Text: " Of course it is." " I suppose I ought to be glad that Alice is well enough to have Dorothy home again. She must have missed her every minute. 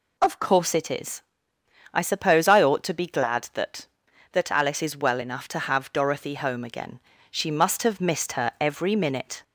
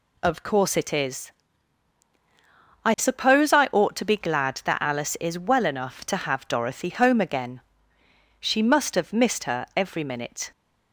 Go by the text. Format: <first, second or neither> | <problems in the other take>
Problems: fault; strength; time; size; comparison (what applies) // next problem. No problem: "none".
second | says "that" twice; at 4.3 s